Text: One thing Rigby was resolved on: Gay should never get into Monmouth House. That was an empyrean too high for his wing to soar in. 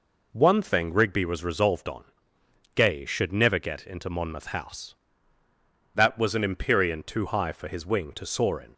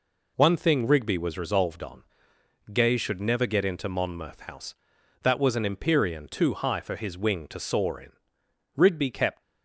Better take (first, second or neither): first